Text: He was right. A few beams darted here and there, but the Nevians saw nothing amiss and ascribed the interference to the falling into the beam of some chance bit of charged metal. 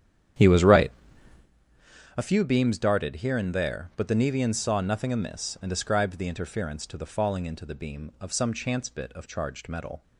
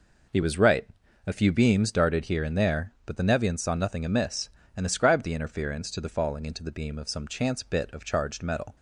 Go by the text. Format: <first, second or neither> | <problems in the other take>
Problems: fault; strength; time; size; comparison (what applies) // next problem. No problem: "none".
second | starts louder than the rest; strong; until 1.5 s; 9.5 dB